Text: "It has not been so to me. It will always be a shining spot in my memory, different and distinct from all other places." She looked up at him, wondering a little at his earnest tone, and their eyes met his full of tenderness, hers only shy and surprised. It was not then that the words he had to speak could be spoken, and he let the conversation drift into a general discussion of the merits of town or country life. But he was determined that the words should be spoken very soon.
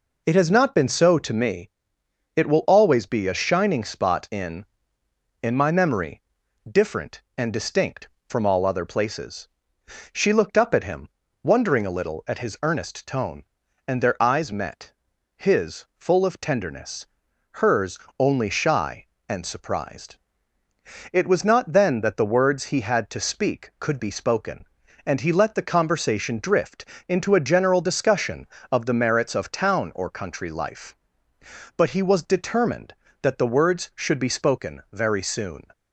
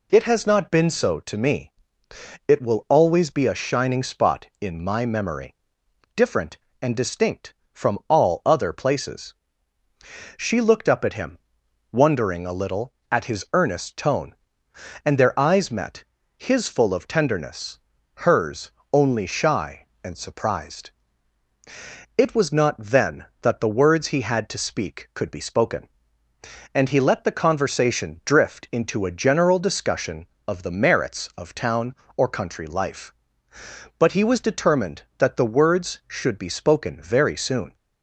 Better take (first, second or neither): second